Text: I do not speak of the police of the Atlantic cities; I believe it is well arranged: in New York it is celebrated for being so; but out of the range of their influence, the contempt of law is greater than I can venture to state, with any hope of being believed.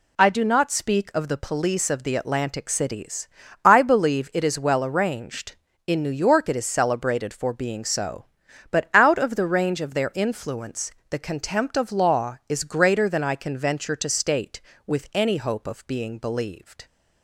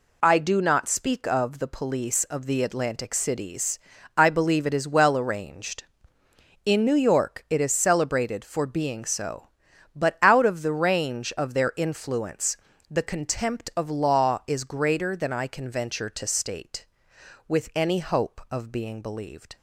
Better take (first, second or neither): neither